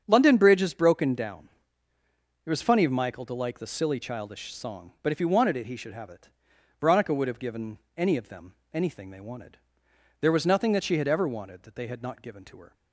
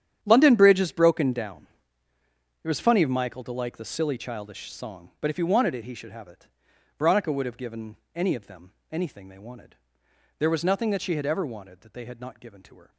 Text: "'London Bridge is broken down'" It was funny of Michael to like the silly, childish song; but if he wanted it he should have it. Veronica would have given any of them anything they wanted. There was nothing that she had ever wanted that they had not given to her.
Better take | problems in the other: first | gets quieter; strong; throughout; 14.5 dB // starts louder than the rest; strong; until 1.2 s; 9.5 dB; strong in the first // pauses between "down" and "It"; noticeable; at 1.6 s; 0.98 s long; noticeable in the first // pauses between "given" and "any"; slight; at 7.9 s; 0.18 s long; slight in the first // pauses between "them" and "anything"; slight; at 8.6 s; 0.22 s long; slight in the first

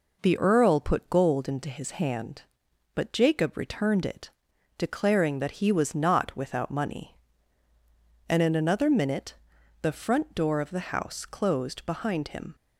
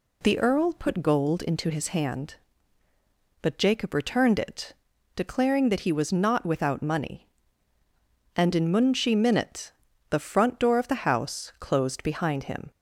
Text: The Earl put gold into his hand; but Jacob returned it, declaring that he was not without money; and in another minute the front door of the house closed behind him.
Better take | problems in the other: first | says "munshi" for "another"; at 8.7 s // pauses between "minute" and "the"; at 9.7 s; 0.38 s long; noticeable in the first

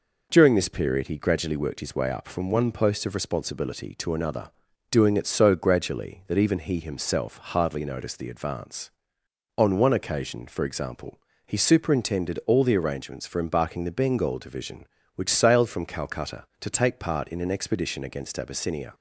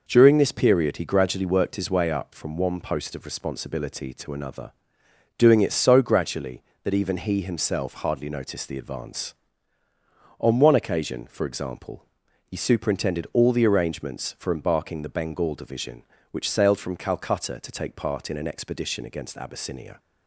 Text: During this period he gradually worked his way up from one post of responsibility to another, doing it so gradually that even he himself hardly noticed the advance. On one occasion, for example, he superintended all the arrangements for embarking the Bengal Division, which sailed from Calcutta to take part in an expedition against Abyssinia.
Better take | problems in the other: neither | none

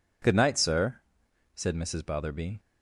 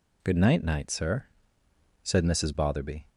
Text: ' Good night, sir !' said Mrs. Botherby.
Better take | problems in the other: first | says "night" twice; at 0.6 s

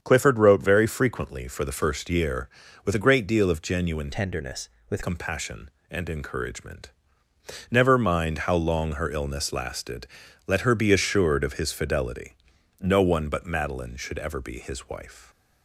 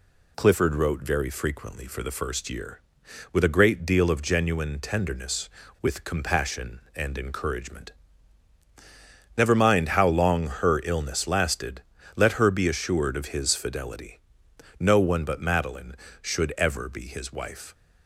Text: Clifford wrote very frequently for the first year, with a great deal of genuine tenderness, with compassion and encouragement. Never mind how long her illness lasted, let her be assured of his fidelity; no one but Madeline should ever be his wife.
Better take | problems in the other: second | starts louder than the rest; strong; until 1.0 s; 7.5 dB // changes voice from "tenderness" to "with"; from 4.1 to 5.0 s; 0.9 s long

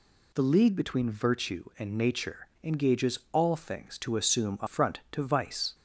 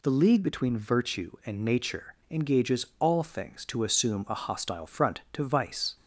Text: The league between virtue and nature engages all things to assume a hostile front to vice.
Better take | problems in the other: second | pauses between "nature" and "engages"; slight; at 2.4 s; 0.16 s long; slight in the second // skips "hostile"; at 4.6 s

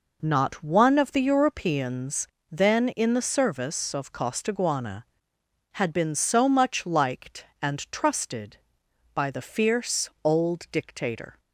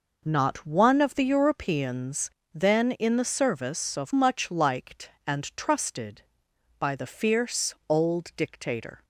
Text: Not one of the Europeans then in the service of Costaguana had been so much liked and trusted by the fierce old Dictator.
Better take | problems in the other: first | pauses between "Europeans" and "then"; slight; at 2.2 s; 0.24 s long; slight in the first // skips "Costaguana had been so"; at 4.1 s

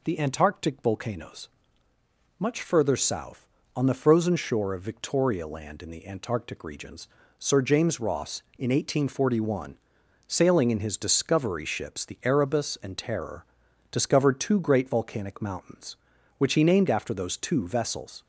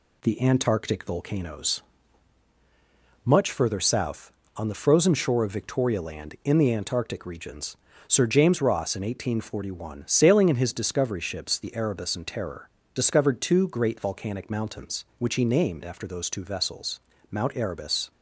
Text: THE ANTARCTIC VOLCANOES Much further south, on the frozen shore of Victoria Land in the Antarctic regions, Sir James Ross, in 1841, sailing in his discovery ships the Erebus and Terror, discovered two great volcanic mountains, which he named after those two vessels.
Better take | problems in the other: first | pauses between "VOLCANOES" and "Much"; strong; at 1.8 s; 1.4 s long; noticeable in the first // goes on to say "Mount Erebus"; noticeable; from 17.3 s on; 0.80 s long

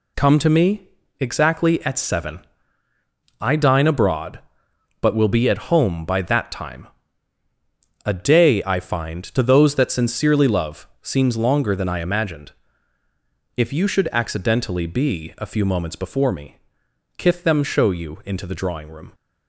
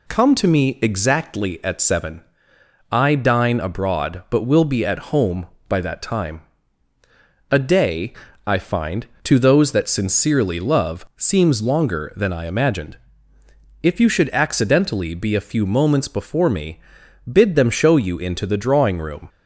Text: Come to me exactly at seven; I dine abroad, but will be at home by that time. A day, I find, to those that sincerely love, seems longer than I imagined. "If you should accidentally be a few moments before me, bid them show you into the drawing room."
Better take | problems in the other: second | pauses between "me" and "exactly"; slight; at 0.8 s; 0.30 s long // says "kith" for "bid"; at 17.1 s

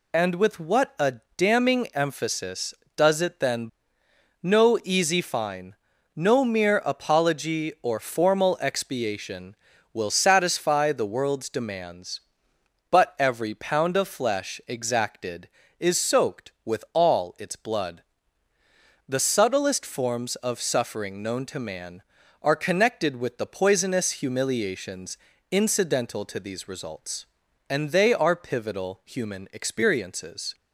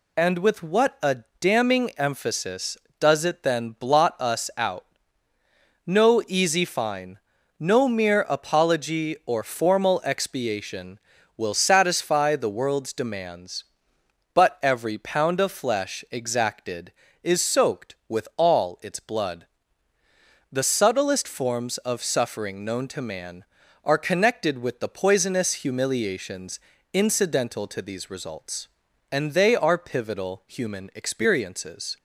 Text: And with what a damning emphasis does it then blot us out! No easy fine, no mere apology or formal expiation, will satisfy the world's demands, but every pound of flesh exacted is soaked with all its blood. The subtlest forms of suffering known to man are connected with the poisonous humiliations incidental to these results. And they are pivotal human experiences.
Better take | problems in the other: second | pauses between "a" and "damning"; slight; at 1.1 s; 0.22 s long; slight in the second // skips "blot us out"; at 4.0 s // pauses between "humiliations" and "incidental"; slight; at 25.1 s; 0.34 s long; slight in the second

